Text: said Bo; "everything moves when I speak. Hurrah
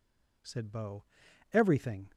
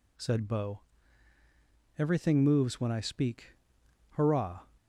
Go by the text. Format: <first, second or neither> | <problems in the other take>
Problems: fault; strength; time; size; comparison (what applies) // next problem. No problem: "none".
second | stops before "moves when I speak Hurrah"; at 2.1 s